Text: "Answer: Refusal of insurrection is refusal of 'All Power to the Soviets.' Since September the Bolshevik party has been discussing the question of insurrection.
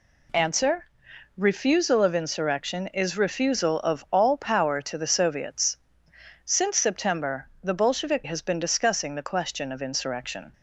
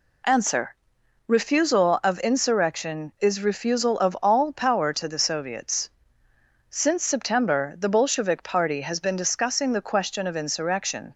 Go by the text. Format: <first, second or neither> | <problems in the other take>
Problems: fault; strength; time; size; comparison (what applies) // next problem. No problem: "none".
second | pauses between "September" and "the"; slight; at 7.4 s; 0.16 s long // skips "party"; at 8.2 s